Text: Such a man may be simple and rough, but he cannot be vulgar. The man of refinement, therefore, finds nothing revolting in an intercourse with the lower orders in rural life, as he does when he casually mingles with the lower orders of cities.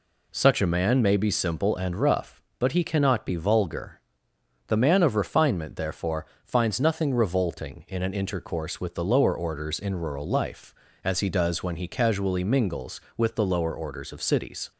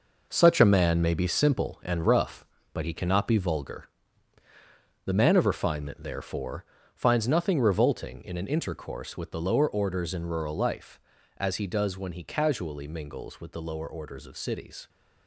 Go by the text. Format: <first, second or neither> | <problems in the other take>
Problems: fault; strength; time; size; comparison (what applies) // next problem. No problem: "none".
first | gets quieter; strong; throughout; 9 dB